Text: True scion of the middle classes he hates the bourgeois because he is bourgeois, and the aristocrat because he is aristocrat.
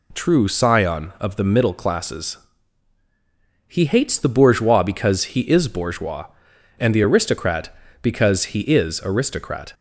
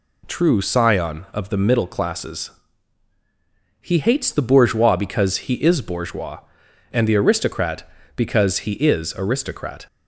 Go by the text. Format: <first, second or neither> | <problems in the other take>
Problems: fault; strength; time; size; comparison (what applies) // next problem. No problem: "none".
neither | pauses between "classes" and "he"; strong; the same in both